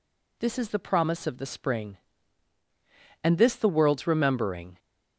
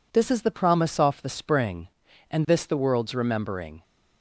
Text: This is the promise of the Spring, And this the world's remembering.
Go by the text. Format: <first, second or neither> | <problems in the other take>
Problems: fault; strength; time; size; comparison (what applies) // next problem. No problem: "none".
first | says "off" for "of"; at 0.9 s